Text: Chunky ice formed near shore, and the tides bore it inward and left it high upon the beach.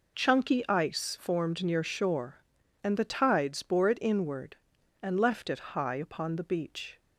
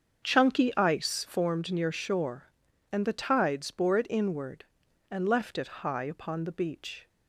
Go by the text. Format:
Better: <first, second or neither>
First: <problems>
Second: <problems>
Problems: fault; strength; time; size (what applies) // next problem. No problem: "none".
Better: first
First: none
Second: starts louder than the rest; until 1.6 s; 7 dB